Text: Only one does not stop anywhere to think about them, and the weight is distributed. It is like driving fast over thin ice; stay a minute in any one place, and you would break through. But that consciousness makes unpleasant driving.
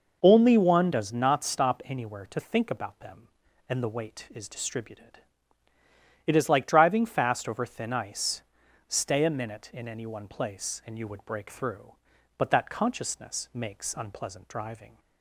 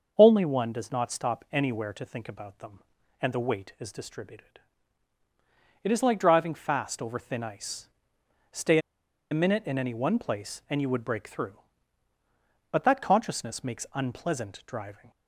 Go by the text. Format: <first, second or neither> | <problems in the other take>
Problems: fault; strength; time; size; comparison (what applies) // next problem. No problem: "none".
first | starts louder than the rest; until 1.1 s; 6.5 dB // pauses between "stay" and "a"; noticeable; at 8.7 s; 0.52 s long